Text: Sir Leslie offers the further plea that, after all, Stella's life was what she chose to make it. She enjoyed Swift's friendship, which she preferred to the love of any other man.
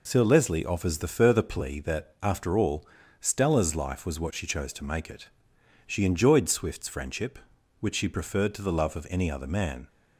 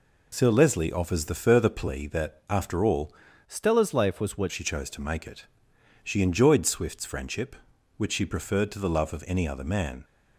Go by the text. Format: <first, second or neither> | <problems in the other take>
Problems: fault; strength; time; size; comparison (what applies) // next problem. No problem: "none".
first | changes voice from "Stella's" to "what"; from 3.4 to 4.5 s; 1.1 s long